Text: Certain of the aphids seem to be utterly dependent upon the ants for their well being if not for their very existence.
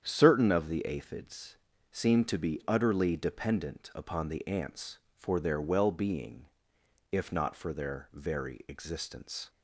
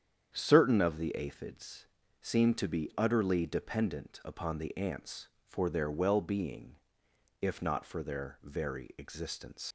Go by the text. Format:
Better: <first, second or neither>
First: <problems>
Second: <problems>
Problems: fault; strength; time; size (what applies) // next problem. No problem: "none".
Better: first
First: starts louder than the rest; strong; until 1.0 s; 8.5 dB // pauses between "aphids" and "seem"; slight; at 1.5 s; 0.34 s long // pauses between "being" and "if"; noticeable; at 6.4 s; 0.62 s long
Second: starts louder than the rest; strong; until 1.3 s; 8.5 dB // pauses between "aphids" and "seem"; slight; at 1.8 s; 0.34 s long // pauses between "being" and "if"; noticeable; at 6.7 s; 0.62 s long // leaves "existence" unfinished; at 9.6 s; 85 ms